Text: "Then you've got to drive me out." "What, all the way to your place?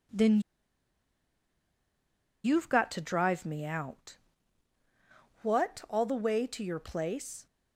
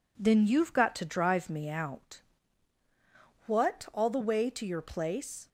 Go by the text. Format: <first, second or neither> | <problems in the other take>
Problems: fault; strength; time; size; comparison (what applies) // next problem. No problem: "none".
second | pauses between "Then" and "you've"; strong; at 0.3 s; 2.0 s long